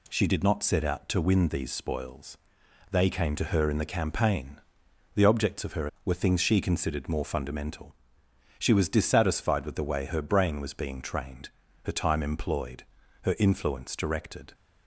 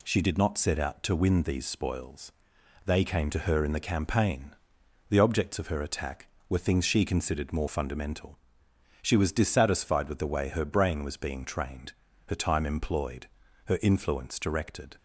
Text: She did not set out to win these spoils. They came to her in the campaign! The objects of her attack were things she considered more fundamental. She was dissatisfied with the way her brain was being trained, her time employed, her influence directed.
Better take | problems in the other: second | skips "attack"; at 5.9 s

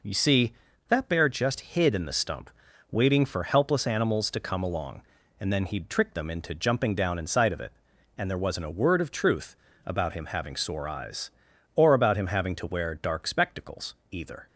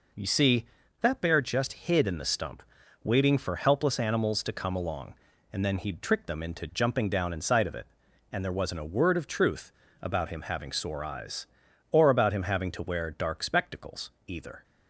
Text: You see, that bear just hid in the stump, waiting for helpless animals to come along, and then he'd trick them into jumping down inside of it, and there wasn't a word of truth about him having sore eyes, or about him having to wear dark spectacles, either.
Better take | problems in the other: neither | pauses between "truth" and "about"; slight; the same in both

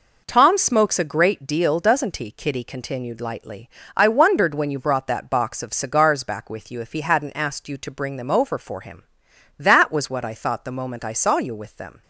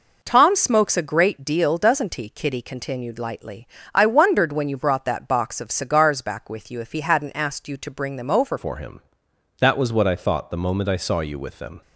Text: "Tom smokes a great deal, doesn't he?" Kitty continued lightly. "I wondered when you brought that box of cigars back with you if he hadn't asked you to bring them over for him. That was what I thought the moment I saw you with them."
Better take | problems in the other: first | changes voice at "for"; from 8.5 s on; 3.3 s long

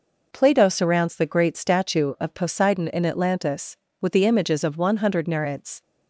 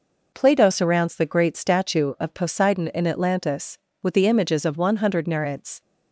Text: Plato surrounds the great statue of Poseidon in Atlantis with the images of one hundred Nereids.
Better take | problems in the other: neither | none

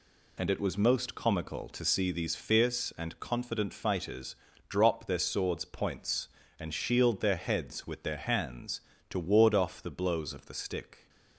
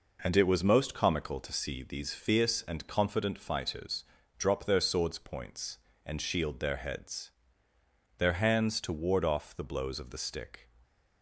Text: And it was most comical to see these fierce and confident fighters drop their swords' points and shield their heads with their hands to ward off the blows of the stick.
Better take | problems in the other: first | pauses between "fighters" and "drop"; slight; at 4.0 s; 0.32 s long; slight in the first // skips "with"; at 7.7 s // stays silent after the last word; slight; from 10.6 s on; 0.6 s long

